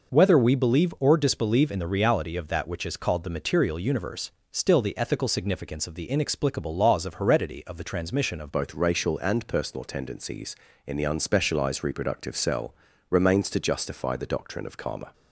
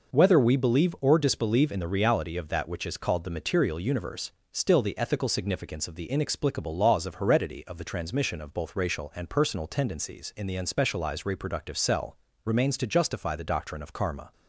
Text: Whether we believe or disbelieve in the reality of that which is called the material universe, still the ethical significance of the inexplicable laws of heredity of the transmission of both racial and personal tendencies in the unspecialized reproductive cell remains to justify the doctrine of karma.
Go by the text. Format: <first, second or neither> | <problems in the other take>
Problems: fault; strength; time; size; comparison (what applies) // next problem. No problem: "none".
second | changes voice at "both"; from 8.5 s on; 6.6 s long // pauses between "cell" and "remains"; at 12.7 s; 0.38 s long; slight in the second